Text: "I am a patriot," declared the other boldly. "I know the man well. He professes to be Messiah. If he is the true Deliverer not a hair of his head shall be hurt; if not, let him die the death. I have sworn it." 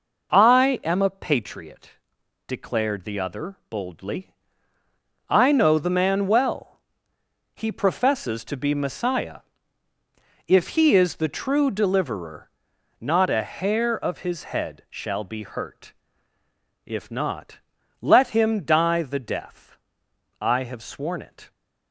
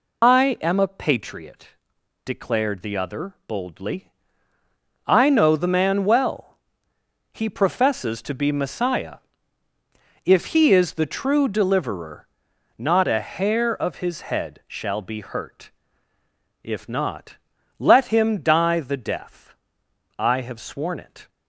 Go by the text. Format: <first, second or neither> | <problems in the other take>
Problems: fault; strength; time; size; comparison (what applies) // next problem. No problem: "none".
first | loses the start of "I"; at 0.2 s; 135 ms // pauses between "Deliverer" and "not"; noticeable; at 12.2 s; 0.52 s long; noticeable in the first